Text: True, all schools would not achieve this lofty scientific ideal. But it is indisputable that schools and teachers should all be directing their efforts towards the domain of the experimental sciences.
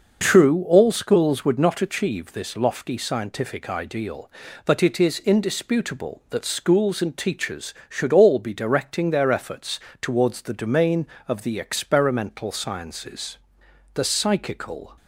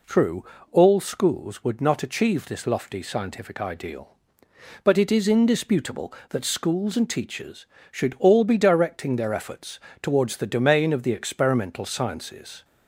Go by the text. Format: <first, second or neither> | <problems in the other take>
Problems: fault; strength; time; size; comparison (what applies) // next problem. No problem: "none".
second | starts louder than the rest; noticeable; until 1.2 s; 6 dB // pauses between "efforts" and "towards"; slight; at 9.7 s; 0.20 s long; slight in the second // goes on to say "The psychical"; noticeable; from 13.9 s on; 1.0 s long